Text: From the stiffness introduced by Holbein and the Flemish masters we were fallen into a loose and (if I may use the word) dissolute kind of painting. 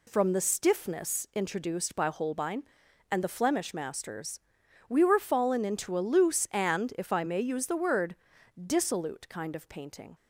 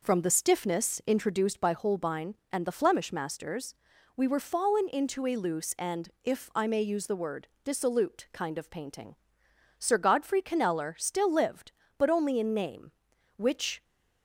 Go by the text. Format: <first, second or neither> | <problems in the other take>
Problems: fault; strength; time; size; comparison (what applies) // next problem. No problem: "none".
first | pauses between "masters" and "we"; at 3.7 s; 0.40 s long; noticeable in the first // goes on to say "Sir Godfrey Kneller still lived but only in name which"; strong; from 9.7 s on; 4.0 s long